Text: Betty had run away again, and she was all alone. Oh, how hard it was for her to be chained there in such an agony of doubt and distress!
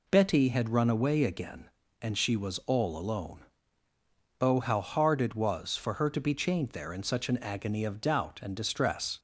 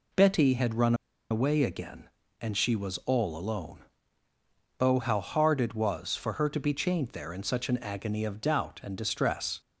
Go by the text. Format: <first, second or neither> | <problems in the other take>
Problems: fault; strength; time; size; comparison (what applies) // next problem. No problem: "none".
first | pauses between "run" and "away"; at 0.9 s; 0.36 s long